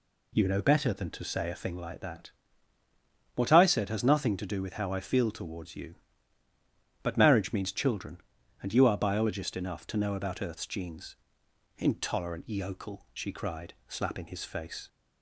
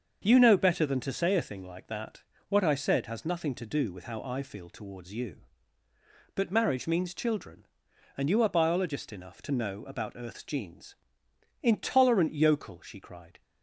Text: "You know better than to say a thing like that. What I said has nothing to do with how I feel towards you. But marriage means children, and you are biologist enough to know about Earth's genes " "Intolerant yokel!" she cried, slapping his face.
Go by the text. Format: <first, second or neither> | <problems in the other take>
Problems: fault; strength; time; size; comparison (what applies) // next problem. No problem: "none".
first | starts louder than the rest; until 1.2 s; 6.5 dB // stops before "slapping his face"; at 13.4 s